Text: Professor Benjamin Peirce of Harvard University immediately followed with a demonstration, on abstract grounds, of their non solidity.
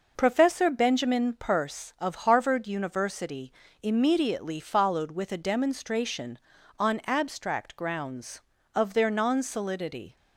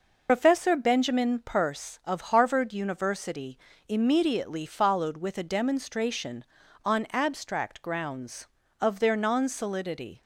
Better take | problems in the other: first | loses the start of "Professor"; at 0.2 s; 80 ms // pauses between "University" and "immediately"; slight; at 3.5 s; 0.30 s long; slight in the first

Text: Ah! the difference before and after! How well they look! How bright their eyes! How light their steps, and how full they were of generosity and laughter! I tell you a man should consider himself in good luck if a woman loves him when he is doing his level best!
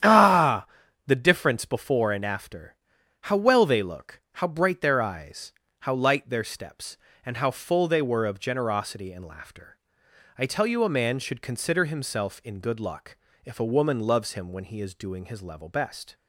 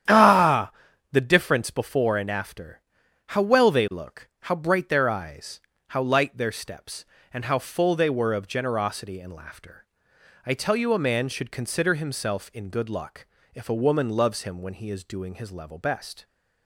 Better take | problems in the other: neither | starts louder than the rest; strong; the same in both // pauses between "luck" and "if"; slight; the same in both

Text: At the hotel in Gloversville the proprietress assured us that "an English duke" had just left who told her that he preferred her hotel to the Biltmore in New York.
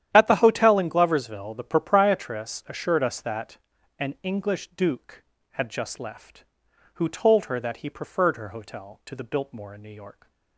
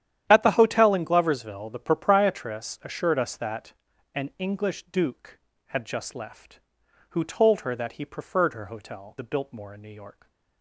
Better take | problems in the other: first | starts louder than the rest; strong; until 1.3 s; 10.5 dB; strong in the first // pauses between "that" and "an"; at 3.7 s; 0.40 s long; also in the first // skips "to"; at 9.1 s

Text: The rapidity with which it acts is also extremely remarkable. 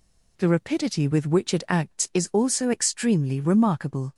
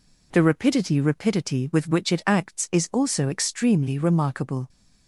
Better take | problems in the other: first | says "rapidity" twice; at 1.0 s

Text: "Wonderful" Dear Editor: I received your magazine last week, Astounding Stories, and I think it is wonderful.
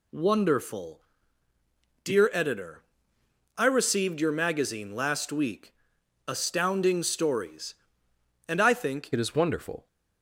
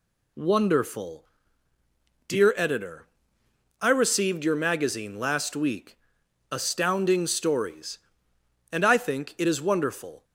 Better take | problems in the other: second | pauses between "Wonderful" and "Dear"; at 1.0 s; 1.0 s long; also in the second // changes voice at "it"; from 9.1 s on; 0.7 s long

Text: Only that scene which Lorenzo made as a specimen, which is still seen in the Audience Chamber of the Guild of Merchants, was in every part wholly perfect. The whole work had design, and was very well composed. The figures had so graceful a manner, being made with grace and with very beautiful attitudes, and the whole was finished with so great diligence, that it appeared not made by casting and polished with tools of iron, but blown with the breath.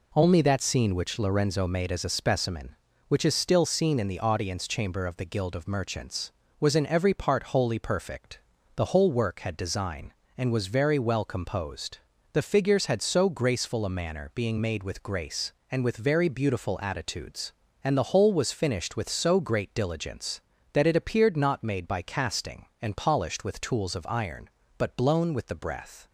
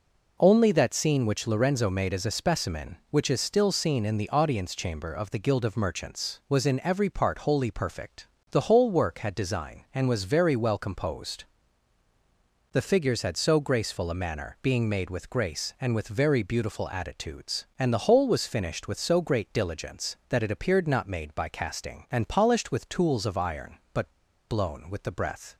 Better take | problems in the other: first | pauses between "but" and "blown"; at 24.1 s; 0.37 s long

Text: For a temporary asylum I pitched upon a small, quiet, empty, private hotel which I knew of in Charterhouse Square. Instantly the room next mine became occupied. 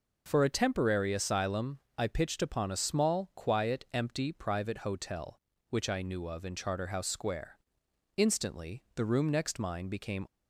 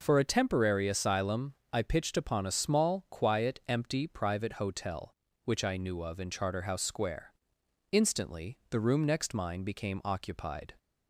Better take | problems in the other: second | pauses between "asylum" and "I"; slight; at 1.7 s; 0.18 s long; slight in the second // stops before "occupied"; at 10.2 s

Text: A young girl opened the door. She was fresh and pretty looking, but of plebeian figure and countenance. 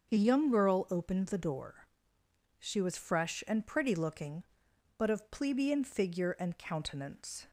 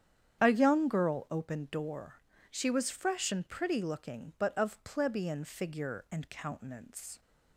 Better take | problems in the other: first | starts louder than the rest; strong; until 1.4 s; 9 dB; also in the first // skips "the"; at 1.6 s

